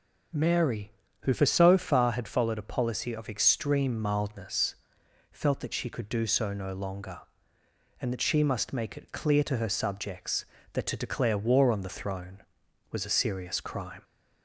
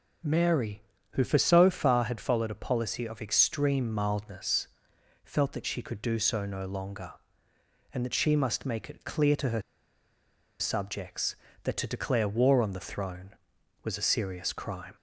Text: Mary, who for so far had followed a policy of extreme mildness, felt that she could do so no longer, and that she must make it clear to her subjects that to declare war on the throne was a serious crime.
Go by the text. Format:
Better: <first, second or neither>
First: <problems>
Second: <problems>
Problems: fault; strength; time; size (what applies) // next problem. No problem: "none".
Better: first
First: none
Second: pauses between "her" and "subjects"; at 9.6 s; 0.99 s long